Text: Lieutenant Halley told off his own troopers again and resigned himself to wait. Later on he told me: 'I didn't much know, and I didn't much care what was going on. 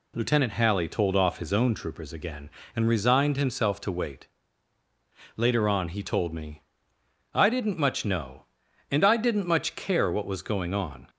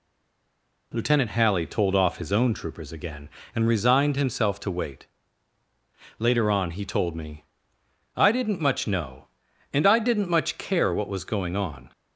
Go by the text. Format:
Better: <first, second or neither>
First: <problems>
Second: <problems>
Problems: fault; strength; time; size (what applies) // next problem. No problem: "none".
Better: first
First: none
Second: stays silent before the first word; slight; until 0.9 s; 0.9 s long